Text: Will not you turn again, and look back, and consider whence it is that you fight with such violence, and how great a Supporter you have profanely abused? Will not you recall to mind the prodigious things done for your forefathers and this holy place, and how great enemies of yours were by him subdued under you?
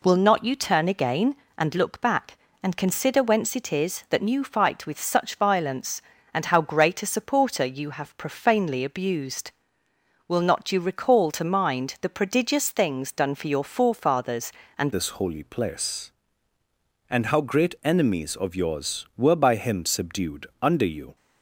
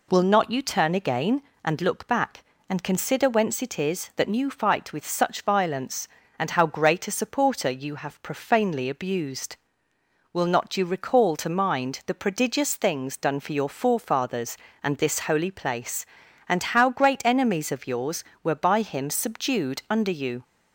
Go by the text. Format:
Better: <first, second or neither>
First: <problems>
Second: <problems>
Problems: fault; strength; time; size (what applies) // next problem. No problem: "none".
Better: second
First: changes voice at "this"; from 14.9 s on; 6.2 s long // pauses between "subdued" and "under"; slight; at 20.4 s; 0.16 s long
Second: none